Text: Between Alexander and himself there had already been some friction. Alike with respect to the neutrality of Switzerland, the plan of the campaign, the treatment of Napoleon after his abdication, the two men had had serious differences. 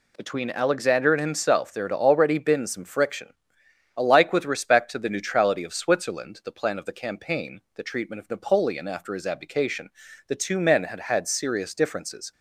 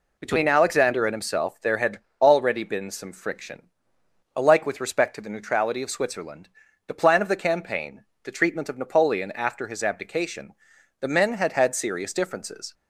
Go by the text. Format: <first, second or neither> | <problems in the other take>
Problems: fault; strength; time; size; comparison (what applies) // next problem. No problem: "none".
first | pauses between "had" and "already"; slight; at 1.9 s; 0.20 s long // skips "two"; at 11.0 s